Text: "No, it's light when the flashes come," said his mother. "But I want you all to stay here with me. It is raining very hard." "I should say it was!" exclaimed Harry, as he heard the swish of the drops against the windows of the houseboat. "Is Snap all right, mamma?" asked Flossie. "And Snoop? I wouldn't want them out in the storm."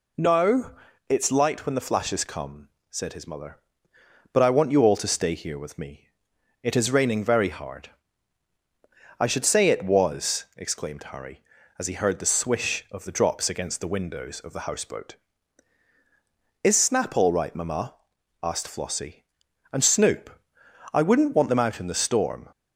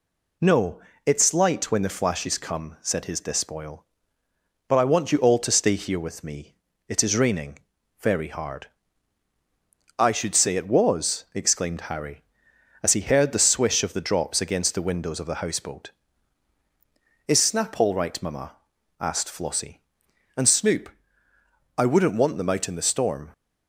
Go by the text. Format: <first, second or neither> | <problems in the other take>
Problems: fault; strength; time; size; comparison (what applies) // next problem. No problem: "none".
first | says "despoil" for "mother"; at 3.2 s // pauses between "raining" and "very"; at 7.5 s; 0.42 s long